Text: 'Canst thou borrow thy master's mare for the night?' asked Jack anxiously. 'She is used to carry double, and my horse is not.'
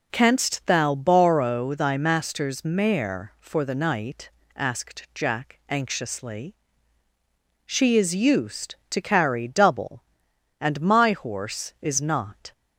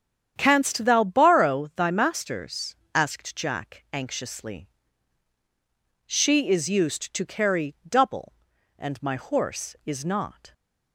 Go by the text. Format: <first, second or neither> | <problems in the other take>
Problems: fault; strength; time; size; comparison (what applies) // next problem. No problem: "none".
first | starts louder than the rest; strong; until 1.3 s; 8.5 dB // skips "mare for the night"; at 2.8 s // pauses between "carry" and "double"; slight; at 7.7 s; 0.16 s long